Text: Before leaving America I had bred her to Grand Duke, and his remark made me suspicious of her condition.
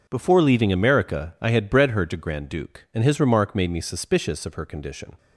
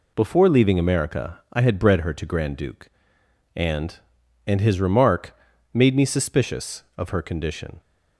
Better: first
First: none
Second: says "and" twice; at 4.4 s // pauses between "remark" and "made"; slight; at 5.3 s; 0.36 s long

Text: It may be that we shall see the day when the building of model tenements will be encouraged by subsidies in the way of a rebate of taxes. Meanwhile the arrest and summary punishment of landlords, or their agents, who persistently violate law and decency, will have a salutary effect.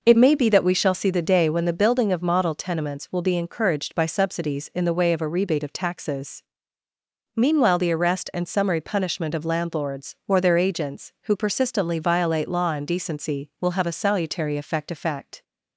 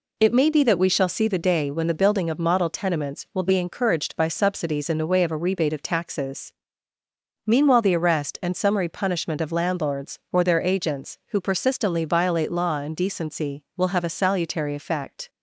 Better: second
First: says "effect" twice; at 14.8 s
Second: none

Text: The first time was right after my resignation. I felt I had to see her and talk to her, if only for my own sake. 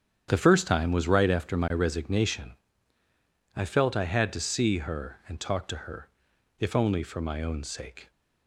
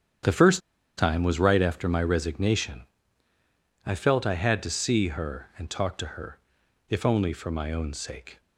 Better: first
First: starts louder than the rest; strong; until 1.3 s; 9 dB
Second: starts louder than the rest; strong; until 1.6 s; 9 dB // pauses between "first" and "time"; at 0.6 s; 0.38 s long

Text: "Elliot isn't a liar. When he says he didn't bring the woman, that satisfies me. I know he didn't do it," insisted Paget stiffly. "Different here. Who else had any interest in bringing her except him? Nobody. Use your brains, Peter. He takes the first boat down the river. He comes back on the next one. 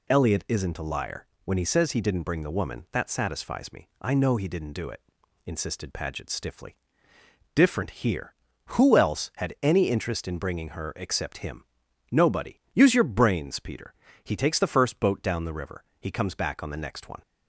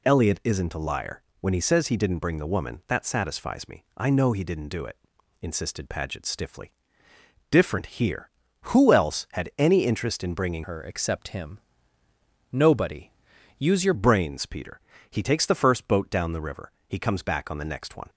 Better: first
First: none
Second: changes voice from "her" to "your"; from 10.6 to 13.9 s; 3.3 s long

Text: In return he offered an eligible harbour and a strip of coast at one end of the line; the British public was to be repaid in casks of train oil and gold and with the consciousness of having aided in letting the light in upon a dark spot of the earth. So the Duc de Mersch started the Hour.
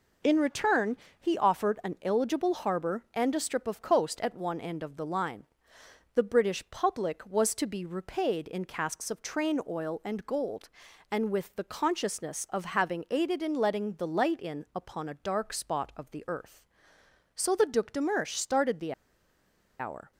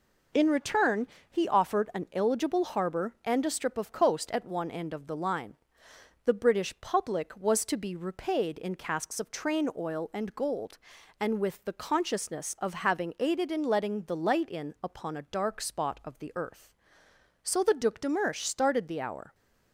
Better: second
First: pauses between "return" and "he"; slight; at 0.9 s; 0.22 s long // pauses between "the" and "Hour"; noticeable; at 18.9 s; 0.87 s long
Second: pauses between "return" and "he"; slight; at 1.0 s; 0.22 s long

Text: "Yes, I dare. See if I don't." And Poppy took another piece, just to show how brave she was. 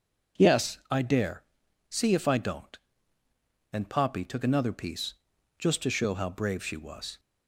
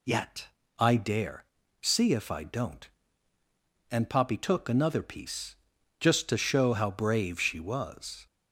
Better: first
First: none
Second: says "Yet" for "Yes"; at 0.0 s

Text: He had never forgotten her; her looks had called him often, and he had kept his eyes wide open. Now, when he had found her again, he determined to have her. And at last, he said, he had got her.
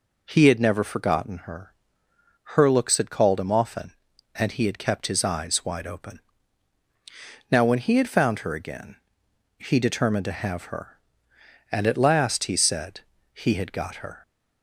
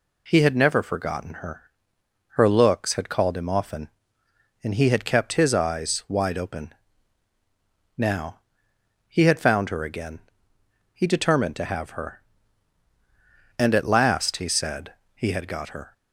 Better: first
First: none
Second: skips "when"; at 8.7 s

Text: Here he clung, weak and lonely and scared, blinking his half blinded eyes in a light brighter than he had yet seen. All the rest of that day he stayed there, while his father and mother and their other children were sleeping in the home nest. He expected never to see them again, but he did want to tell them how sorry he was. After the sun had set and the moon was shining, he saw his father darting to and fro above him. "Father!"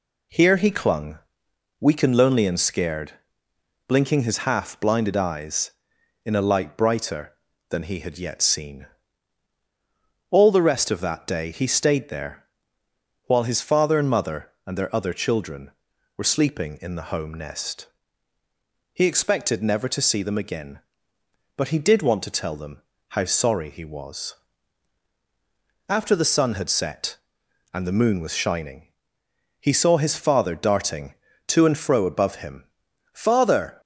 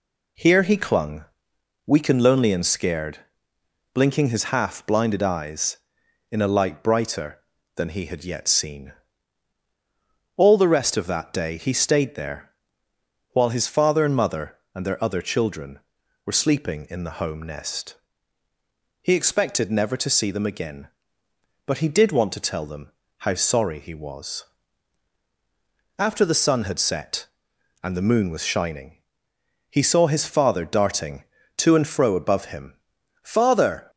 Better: neither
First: pauses between "them" and "how"; slight; at 22.8 s; 0.28 s long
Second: pauses between "them" and "how"; slight; at 22.9 s; 0.28 s long

